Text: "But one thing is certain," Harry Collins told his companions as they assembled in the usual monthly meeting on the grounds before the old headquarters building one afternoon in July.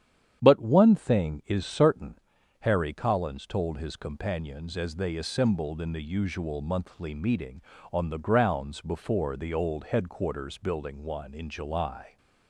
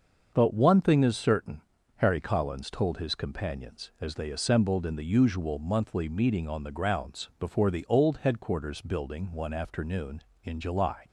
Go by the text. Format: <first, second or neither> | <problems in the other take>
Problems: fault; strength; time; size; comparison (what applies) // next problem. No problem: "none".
second | starts louder than the rest; strong; until 1.4 s; 9.5 dB; also in the second // skips "afternoon"; at 11.3 s